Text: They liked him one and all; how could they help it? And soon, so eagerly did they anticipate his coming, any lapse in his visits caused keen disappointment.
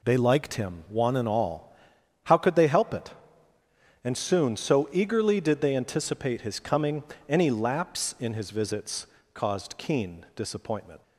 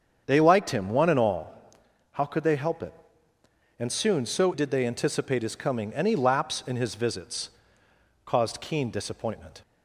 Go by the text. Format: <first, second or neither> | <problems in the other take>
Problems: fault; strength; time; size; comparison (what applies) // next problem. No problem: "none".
first | starts louder than the rest; strong; until 1.2 s; 7.5 dB // skips "eagerly"; at 4.5 s // pauses between "visits" and "caused"; noticeable; at 7.4 s; 0.76 s long; slight in the first